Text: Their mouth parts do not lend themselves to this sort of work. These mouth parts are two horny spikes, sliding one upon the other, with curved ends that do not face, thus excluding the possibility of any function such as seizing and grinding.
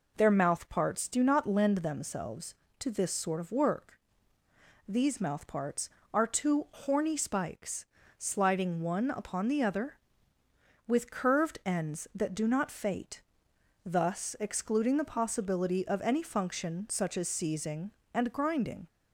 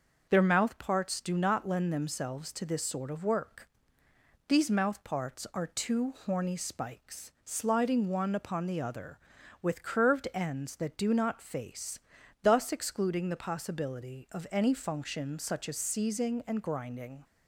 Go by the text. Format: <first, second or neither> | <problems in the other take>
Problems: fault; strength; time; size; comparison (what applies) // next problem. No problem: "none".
second | says "fate" for "face"; at 12.7 s